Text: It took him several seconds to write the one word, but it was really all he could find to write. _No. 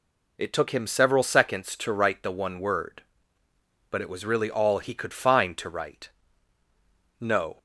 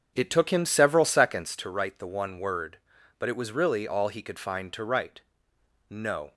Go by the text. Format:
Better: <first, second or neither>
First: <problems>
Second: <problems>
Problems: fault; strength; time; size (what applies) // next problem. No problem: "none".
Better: first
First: none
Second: starts louder than the rest; until 1.6 s; 7 dB